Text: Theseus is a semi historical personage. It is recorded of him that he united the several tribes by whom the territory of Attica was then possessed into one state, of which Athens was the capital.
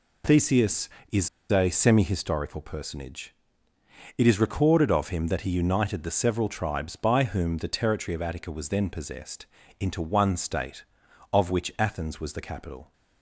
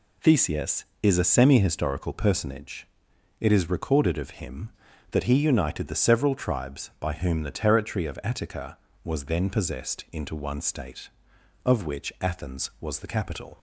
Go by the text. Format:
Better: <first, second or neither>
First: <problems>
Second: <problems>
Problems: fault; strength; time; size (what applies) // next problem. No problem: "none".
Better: second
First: pauses between "is" and "a"; slight; at 1.2 s; 0.21 s long // pauses between "possessed" and "into"; slight; at 9.4 s; 0.34 s long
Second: none